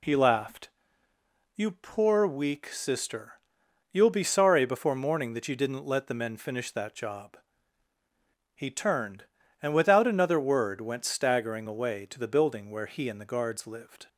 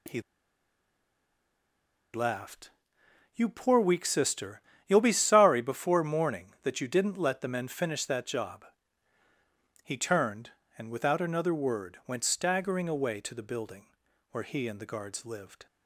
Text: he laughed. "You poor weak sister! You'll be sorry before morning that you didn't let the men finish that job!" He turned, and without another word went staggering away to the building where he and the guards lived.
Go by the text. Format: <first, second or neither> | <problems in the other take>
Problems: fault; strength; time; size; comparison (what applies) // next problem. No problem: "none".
first | pauses between "he" and "laughed"; strong; at 0.2 s; 1.9 s long // pauses between "building" and "where"; at 13.8 s; 0.42 s long